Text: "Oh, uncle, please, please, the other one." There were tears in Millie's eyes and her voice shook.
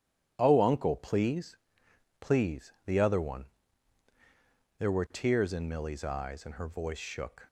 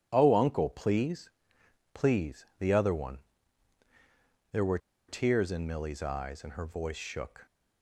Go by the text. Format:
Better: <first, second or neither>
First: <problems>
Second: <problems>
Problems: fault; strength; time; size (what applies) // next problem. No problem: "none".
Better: first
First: none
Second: pauses between "were" and "tears"; slight; at 4.7 s; 0.30 s long